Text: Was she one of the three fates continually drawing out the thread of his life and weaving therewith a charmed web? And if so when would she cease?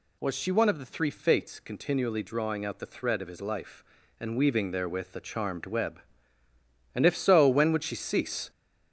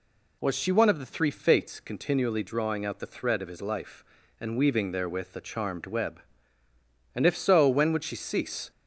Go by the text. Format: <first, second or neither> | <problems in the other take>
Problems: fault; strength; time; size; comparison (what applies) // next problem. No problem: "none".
second | gets louder; noticeable; throughout; 6 dB